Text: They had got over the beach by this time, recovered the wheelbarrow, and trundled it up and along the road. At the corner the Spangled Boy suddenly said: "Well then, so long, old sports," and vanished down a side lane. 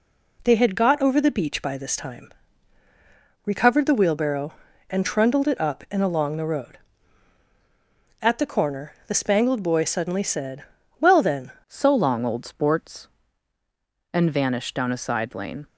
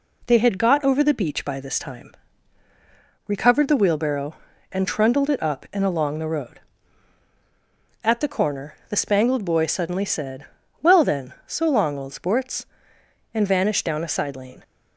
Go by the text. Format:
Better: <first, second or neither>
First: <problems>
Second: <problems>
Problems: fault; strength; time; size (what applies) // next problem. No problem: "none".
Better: second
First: changes voice at "so"; from 11.6 s on; 4.0 s long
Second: none